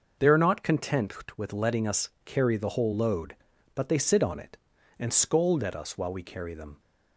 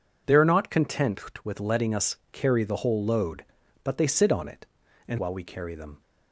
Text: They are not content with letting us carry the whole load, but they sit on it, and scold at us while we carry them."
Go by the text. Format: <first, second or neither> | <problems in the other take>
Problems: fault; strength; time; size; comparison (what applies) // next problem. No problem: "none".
first | pauses between "us" and "carry"; slight; at 2.1 s; 0.16 s long; slight in the first // skips "scold at us"; at 5.1 s